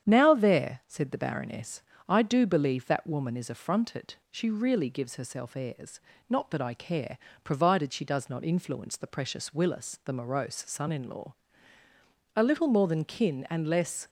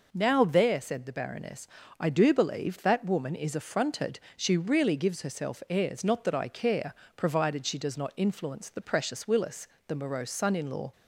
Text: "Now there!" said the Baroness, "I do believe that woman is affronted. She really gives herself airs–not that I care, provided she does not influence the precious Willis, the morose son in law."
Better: second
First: starts louder than the rest; strong; until 1.1 s; 9 dB // goes on to say "A little more than kin and less"; strong; from 12.3 s on; 1.7 s long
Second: none

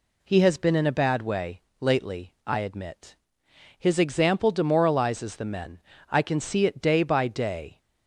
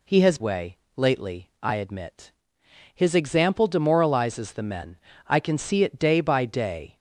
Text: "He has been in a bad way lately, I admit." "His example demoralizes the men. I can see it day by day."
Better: first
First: pauses between "way" and "lately"; slight; at 1.6 s; 0.18 s long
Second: skips "been in a bad"; at 0.3 s // pauses between "way" and "lately"; slight; at 0.7 s; 0.18 s long

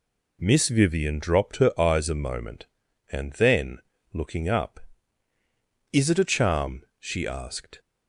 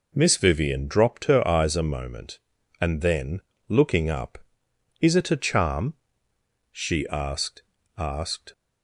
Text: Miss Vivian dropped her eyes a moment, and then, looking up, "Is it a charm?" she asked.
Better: first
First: none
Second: says "asked" twice; at 7.9 s

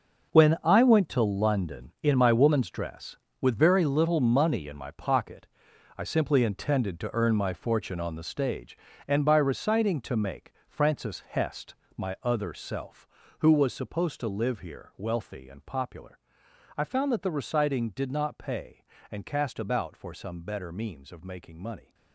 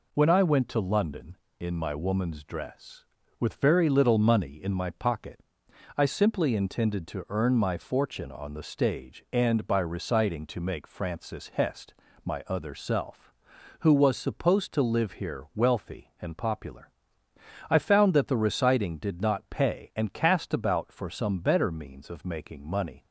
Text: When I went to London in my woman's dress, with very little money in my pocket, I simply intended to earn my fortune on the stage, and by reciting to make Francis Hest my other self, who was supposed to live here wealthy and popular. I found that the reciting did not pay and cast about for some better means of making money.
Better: second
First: gets quieter; strong; throughout; 12.5 dB // pauses between "make" and "Francis"; slight; at 10.5 s; 0.16 s long // pauses between "Hest" and "my"; slight; at 11.7 s; 0.20 s long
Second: pauses between "Hest" and "my"; slight; at 11.9 s; 0.30 s long

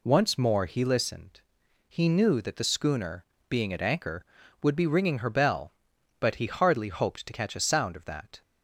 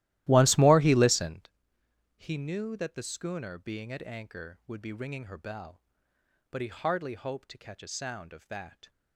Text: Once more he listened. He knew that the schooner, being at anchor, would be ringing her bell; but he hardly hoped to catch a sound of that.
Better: first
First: none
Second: starts louder than the rest; strong; until 1.6 s; 15.5 dB

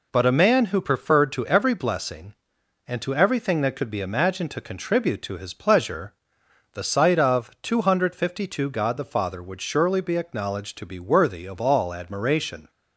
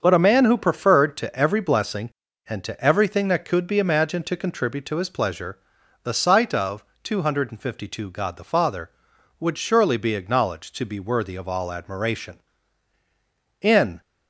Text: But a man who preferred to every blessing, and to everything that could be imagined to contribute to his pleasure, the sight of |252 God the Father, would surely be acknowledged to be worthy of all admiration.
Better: first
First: none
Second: starts louder than the rest; until 1.0 s; 7 dB // goes on to say "In"; slight; from 13.6 s on; 0.40 s long

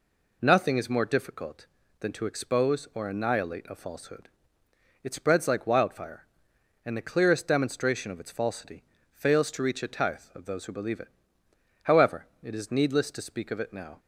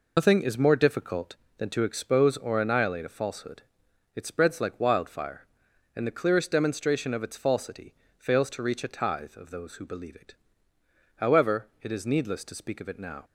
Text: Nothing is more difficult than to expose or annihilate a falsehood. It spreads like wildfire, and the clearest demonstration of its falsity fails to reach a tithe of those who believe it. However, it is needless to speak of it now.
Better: first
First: pauses between "falsity" and "fails"; slight; at 8.8 s; 0.30 s long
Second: loses the start of "Nothing"; at 0.1 s; 95 ms // pauses between "falsity" and "fails"; slight; at 7.9 s; 0.24 s long

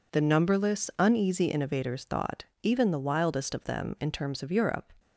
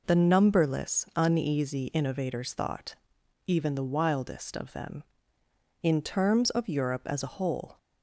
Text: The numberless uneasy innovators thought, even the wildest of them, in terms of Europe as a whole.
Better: second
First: stops before "as a whole"; at 4.9 s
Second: none

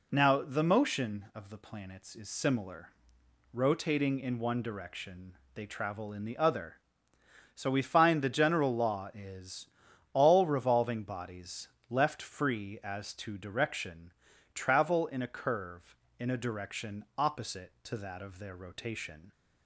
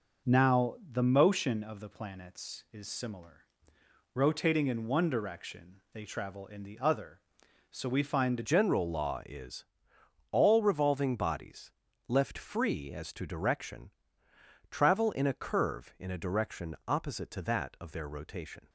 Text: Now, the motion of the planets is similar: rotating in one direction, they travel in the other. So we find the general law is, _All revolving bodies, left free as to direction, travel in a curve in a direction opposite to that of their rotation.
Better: first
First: none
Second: changes voice at "general"; from 8.4 s on; 10.2 s long

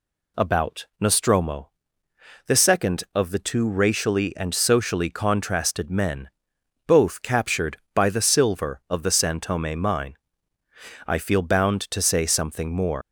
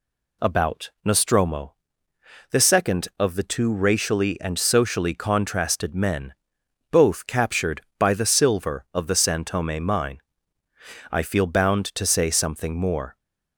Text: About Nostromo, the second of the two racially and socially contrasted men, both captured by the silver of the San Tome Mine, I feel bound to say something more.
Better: second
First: leaves "more" unfinished; at 13.0 s; 130 ms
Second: none

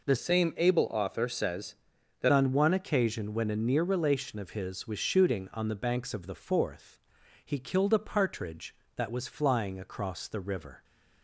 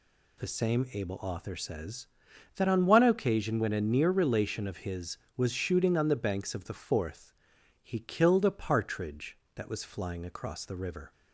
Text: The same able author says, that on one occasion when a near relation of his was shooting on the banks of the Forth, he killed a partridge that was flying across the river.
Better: second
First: changes voice from "same" to "that"; from 0.1 to 2.3 s; 2.2 s long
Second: none

